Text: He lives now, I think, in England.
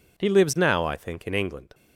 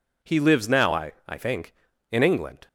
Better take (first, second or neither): first